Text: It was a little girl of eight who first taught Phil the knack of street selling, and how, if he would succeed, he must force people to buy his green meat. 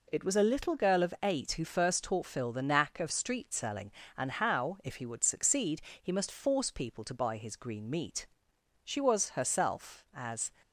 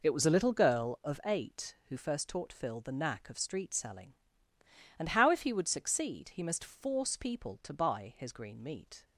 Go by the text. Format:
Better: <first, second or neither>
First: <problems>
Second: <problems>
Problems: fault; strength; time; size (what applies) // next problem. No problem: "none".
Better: second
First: goes on to say "She was herself as"; from 8.8 s on; 1.6 s long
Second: none